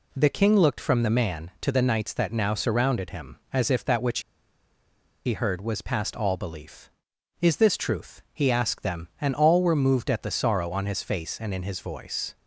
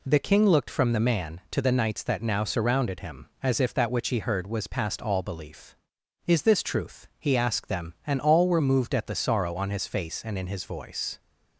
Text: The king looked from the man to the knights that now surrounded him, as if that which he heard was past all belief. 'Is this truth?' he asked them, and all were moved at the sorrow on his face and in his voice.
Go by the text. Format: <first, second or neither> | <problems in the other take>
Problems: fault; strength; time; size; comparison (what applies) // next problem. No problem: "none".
second | pauses between "which" and "he"; at 4.1 s; 1.0 s long